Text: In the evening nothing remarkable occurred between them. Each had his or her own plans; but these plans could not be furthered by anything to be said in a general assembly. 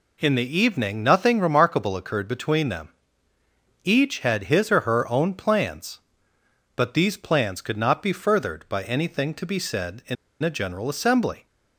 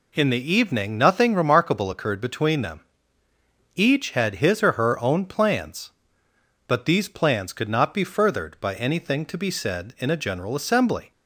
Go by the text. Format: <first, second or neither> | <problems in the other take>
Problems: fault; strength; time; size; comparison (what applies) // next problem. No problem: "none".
second | pauses between "in" and "a"; slight; at 10.1 s; 0.27 s long